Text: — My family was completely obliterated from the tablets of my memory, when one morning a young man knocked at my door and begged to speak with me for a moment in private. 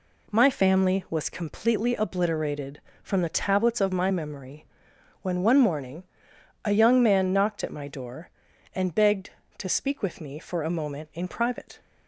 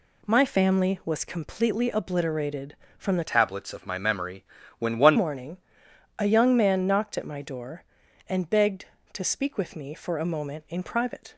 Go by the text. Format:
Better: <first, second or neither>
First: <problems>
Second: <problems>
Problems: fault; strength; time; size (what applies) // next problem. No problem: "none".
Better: first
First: pauses between "morning" and "a"; noticeable; at 6.0 s; 0.62 s long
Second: changes voice from "tablets" to "one"; from 3.2 to 5.1 s; 1.9 s long // pauses between "morning" and "a"; noticeable; at 5.5 s; 0.62 s long